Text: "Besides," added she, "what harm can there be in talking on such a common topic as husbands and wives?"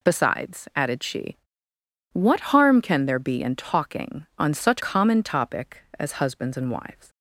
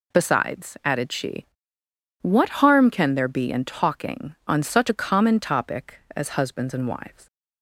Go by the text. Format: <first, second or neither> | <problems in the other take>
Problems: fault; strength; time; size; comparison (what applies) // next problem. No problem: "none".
second | skips "a"; at 4.8 s